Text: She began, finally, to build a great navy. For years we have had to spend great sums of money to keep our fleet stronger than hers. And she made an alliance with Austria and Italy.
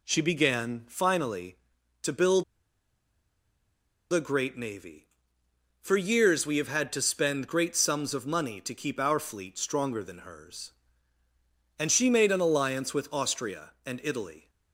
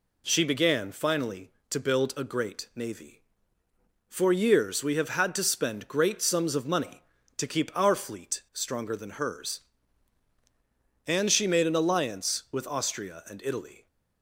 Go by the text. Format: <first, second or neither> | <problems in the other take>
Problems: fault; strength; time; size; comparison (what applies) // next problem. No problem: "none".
second | pauses between "build" and "a"; strong; at 2.4 s; 1.6 s long